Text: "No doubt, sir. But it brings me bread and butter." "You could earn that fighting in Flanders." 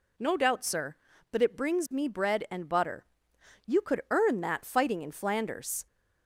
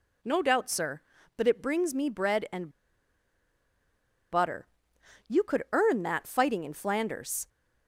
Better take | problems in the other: first | pauses between "and" and "butter"; strong; at 2.6 s; 1.6 s long

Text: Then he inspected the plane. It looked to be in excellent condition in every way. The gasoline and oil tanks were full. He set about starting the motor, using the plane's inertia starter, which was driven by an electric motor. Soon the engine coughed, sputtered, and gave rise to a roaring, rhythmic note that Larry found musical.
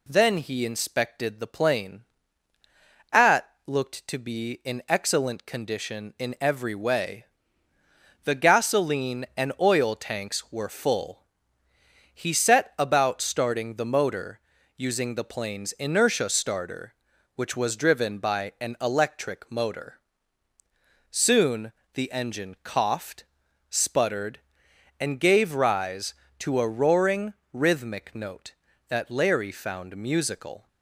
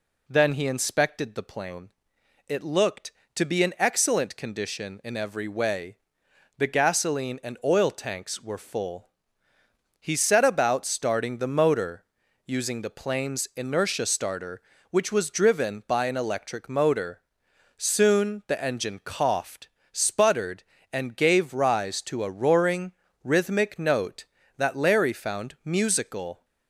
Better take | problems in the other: second | says "At" for "It"; at 3.1 s // pauses between "Soon" and "the"; slight; at 21.7 s; 0.20 s long

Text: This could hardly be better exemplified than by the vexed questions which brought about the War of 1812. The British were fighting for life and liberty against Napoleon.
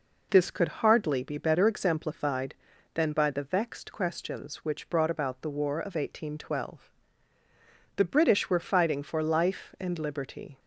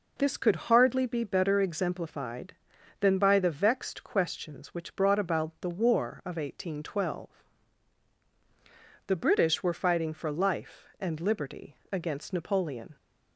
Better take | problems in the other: second | stops before "against Napoleon"; at 10.5 s

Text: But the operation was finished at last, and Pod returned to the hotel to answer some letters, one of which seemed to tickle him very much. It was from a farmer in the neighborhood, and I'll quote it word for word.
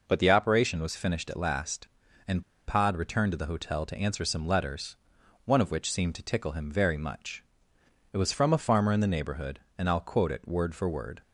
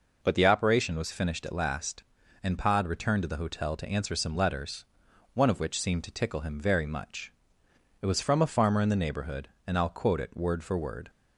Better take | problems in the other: second | pauses between "and" and "Pod"; slight; at 2.4 s; 0.24 s long

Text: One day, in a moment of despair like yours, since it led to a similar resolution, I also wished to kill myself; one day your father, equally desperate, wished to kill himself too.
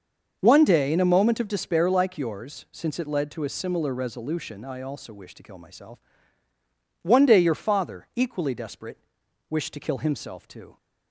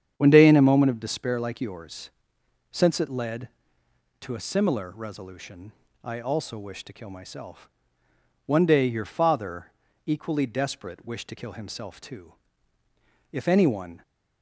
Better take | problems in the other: first | starts louder than the rest; strong; until 1.1 s; 8.5 dB; also in the first // goes on to say "If anyone"; noticeable; from 13.3 s on; 0.70 s long

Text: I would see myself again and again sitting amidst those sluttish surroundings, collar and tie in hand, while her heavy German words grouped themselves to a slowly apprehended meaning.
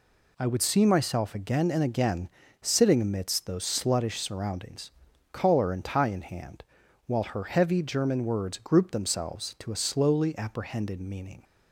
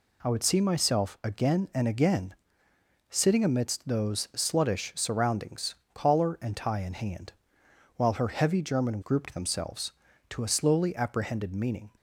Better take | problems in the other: first | pauses between "again" and "sitting"; noticeable; at 2.3 s; 0.74 s long; slight in the first // skips "words"; at 9.0 s

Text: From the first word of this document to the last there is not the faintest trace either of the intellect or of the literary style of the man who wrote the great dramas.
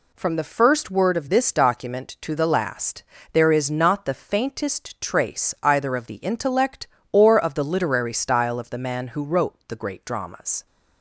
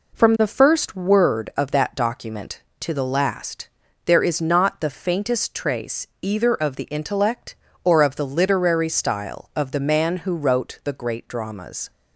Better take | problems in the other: first | says "that" for "this"; at 1.7 s // pauses between "last" and "there"; at 3.6 s; 0.38 s long; slight in the first // pauses between "trace" and "either"; slight; at 6.0 s; 0.16 s long

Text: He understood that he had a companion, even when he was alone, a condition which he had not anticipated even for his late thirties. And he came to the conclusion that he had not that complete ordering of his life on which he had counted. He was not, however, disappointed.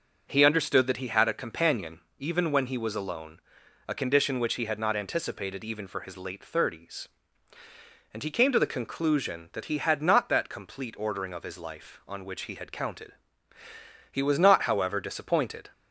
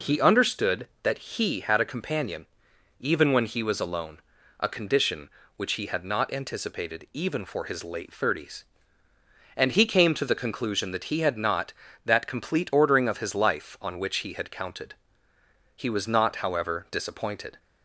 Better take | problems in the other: neither | none

